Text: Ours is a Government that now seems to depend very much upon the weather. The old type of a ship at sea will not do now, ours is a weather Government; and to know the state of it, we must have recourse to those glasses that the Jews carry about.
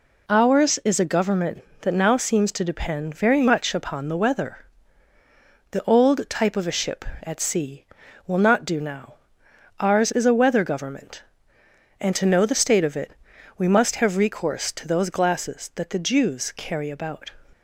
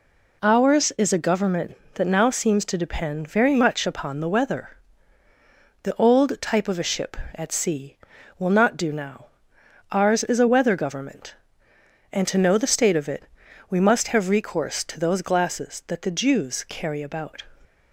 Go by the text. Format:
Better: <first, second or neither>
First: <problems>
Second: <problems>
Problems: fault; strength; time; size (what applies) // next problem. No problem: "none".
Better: neither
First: none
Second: none